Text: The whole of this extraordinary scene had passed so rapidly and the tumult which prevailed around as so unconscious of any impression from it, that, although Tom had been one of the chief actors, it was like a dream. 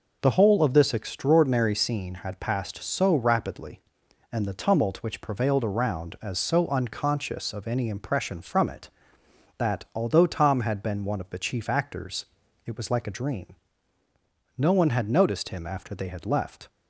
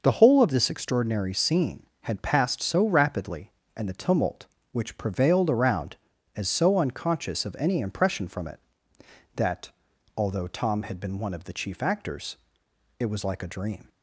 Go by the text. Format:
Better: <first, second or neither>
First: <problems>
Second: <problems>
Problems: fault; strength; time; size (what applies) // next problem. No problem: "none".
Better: second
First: goes on to say "No one had noticed him after they had left"; strong; from 14.5 s on; 2.1 s long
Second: none